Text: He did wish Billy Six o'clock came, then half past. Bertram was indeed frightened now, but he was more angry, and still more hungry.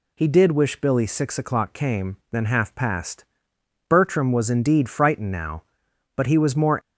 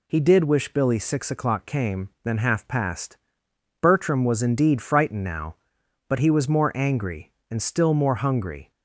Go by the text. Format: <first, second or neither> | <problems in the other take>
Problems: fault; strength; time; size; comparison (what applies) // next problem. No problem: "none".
second | stops before "angry and still more hungry"; at 6.7 s